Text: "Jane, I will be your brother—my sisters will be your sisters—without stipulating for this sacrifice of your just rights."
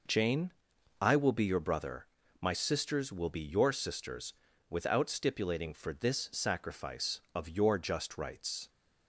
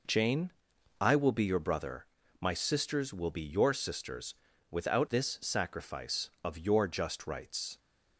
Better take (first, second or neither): first